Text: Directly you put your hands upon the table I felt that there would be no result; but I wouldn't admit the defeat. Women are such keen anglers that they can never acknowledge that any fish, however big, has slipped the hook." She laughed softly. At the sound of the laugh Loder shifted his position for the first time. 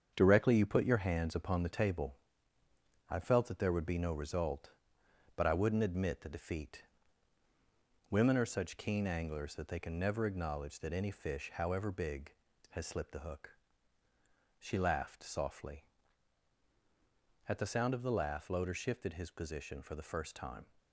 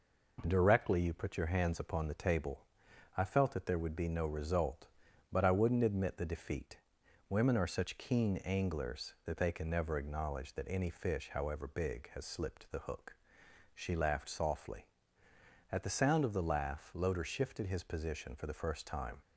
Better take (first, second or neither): second